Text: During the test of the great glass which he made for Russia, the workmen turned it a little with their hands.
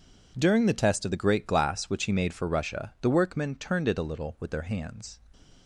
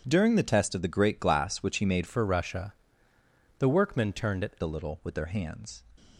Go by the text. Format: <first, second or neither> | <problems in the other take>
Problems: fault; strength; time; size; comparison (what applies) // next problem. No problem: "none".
first | changes voice from "for" to "it"; from 2.0 to 4.5 s; 2.5 s long